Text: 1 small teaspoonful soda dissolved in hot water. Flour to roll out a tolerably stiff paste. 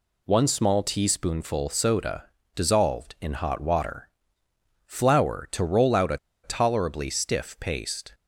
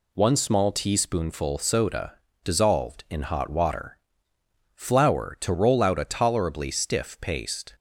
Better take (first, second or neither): second